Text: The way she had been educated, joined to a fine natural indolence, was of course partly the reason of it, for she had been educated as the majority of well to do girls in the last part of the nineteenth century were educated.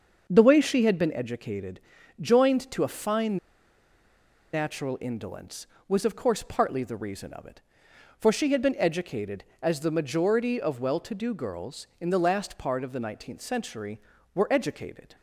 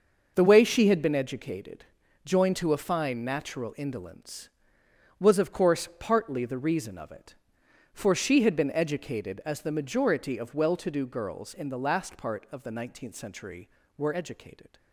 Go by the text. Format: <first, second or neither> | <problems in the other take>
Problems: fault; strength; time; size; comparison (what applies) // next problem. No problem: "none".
second | starts louder than the rest; until 1.2 s; 6.5 dB // pauses between "fine" and "natural"; at 3.3 s; 1.1 s long